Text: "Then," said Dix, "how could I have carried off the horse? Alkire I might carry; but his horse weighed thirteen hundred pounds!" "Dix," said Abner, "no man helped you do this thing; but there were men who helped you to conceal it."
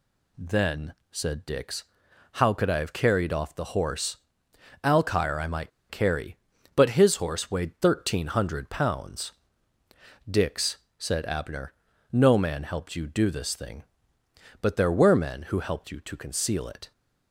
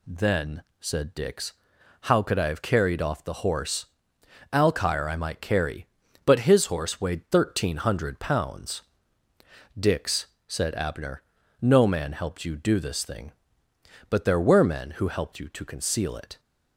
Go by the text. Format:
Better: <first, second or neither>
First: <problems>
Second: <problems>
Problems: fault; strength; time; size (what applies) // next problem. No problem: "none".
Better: second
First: pauses between "might" and "carry"; slight; at 5.7 s; 0.19 s long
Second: none